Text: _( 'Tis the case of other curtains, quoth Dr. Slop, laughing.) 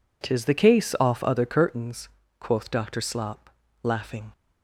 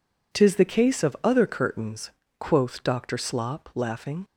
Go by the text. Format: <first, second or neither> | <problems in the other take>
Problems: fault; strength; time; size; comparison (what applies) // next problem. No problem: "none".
second | says "off" for "of"; at 1.0 s